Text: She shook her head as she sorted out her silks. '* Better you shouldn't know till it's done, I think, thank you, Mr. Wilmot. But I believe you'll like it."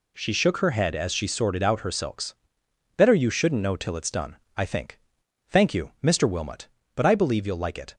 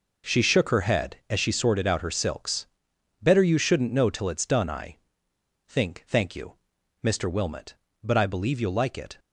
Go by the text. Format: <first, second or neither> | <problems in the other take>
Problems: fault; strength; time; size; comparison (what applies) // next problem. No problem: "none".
first | pauses between "I" and "think"; noticeable; at 4.9 s; 0.70 s long